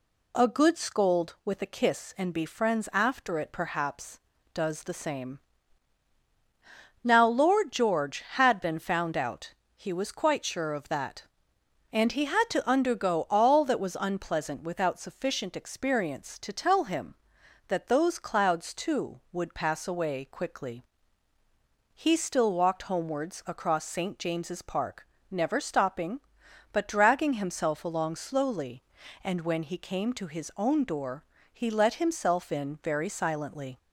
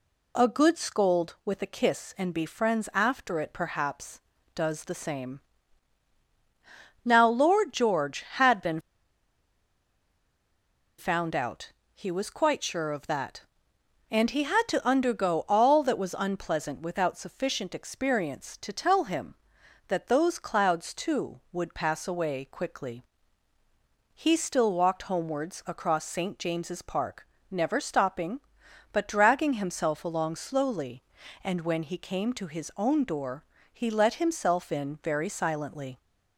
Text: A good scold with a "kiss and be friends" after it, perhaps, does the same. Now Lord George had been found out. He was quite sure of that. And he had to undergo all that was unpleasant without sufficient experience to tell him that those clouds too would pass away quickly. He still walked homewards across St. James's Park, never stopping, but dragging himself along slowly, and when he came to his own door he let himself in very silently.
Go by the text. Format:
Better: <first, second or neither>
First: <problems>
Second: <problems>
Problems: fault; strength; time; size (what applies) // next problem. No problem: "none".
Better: first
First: pauses between "door" and "he"; slight; at 31.2 s; 0.26 s long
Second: pauses between "been" and "found"; strong; at 8.8 s; 2.1 s long // pauses between "door" and "he"; slight; at 33.4 s; 0.26 s long